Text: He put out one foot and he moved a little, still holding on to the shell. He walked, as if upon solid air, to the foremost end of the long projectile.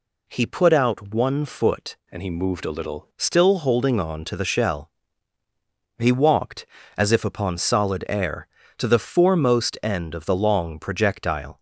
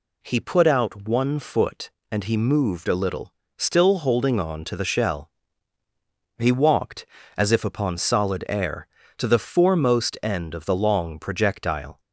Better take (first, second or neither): second